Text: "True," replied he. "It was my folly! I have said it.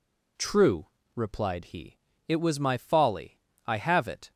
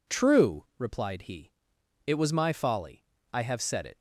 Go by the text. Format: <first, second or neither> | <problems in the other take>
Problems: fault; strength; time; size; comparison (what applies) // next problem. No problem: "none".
second | skips "said"; at 4.0 s